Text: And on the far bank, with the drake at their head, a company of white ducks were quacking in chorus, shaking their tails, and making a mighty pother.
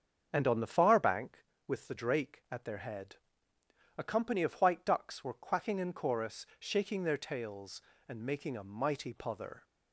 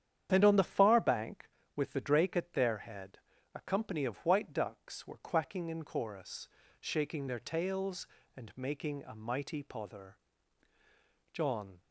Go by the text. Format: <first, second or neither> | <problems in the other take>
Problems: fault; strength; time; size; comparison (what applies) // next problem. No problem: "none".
first | starts louder than the rest; strong; until 1.3 s; 9.5 dB; strong in the first // goes on to say "John"; slight; from 11.3 s on; 0.48 s long